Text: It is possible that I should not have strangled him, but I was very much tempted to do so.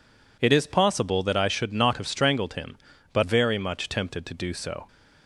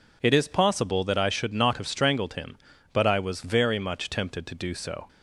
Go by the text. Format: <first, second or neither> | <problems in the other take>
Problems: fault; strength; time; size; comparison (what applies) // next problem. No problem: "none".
second | skips "I was"; at 3.2 s